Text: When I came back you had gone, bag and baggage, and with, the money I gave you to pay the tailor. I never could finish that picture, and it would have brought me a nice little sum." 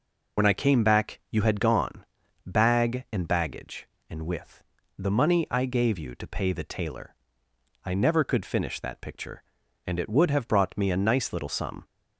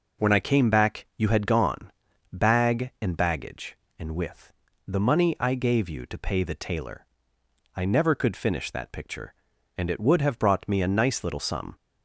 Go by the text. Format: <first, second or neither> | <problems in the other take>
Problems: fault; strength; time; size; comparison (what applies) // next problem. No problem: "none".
second | loses the start of "When"; at 0.3 s; 45 ms